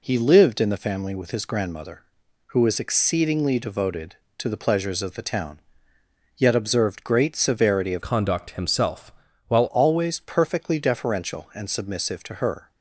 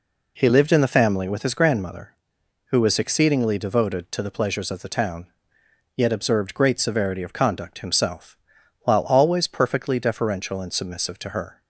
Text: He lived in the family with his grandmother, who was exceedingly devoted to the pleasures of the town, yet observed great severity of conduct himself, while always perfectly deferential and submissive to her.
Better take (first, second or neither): second